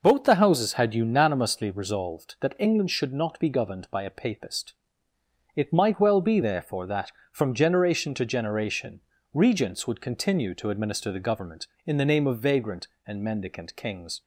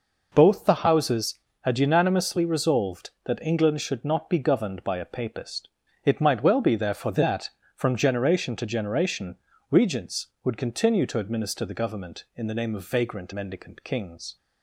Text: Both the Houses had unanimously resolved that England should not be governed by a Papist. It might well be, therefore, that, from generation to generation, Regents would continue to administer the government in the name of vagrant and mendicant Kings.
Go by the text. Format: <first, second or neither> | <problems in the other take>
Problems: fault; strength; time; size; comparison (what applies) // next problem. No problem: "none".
first | skips "and"; at 13.3 s